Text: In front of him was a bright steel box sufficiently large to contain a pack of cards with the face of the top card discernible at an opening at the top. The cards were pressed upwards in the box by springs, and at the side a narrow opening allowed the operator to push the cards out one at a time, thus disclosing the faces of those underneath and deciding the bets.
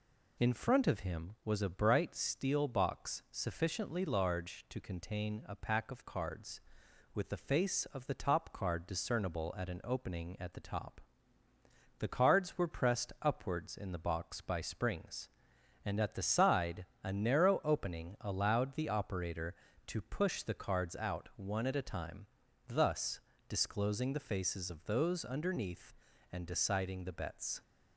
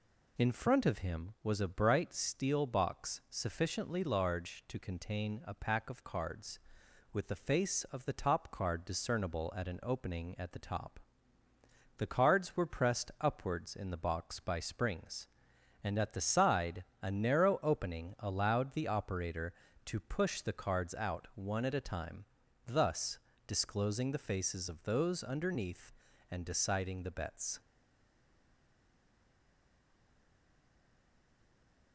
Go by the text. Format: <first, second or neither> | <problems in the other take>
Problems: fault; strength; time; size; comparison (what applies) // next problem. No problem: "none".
first | pauses between "side" and "a"; slight; at 16.8 s; 0.16 s long; slight in the first // pauses between "thus" and "disclosing"; slight; at 23.1 s; 0.28 s long; slight in the first // stays silent after the last word; strong; from 27.6 s on; 4.3 s long